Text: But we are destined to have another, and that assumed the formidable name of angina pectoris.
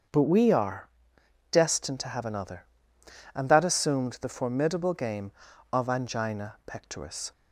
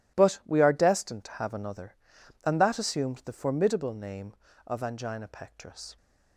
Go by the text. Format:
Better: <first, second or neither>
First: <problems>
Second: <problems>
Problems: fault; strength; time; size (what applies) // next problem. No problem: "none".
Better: second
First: starts louder than the rest; until 1.7 s; 7 dB // pauses between "are" and "destined"; noticeable; at 0.8 s; 0.62 s long // says "game" for "name"; at 4.9 s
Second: none